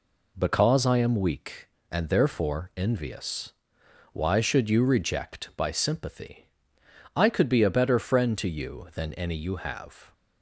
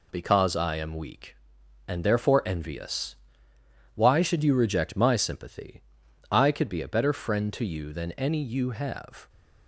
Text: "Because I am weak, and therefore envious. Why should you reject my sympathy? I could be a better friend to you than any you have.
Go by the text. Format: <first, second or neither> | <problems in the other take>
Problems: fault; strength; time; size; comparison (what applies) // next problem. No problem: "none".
second | says "by" for "my"; at 5.5 s